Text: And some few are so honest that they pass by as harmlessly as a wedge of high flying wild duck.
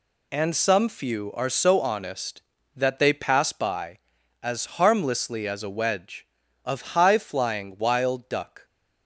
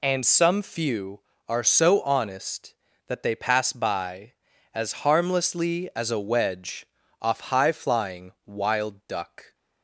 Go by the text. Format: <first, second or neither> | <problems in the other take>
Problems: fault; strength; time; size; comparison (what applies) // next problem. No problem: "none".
first | says "off" for "of"; at 7.2 s